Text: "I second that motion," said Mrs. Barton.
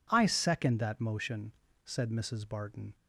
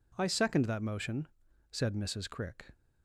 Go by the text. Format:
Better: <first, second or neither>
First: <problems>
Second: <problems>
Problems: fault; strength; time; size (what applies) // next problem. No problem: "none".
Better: first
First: none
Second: says "Crick" for "Barton"; at 2.2 s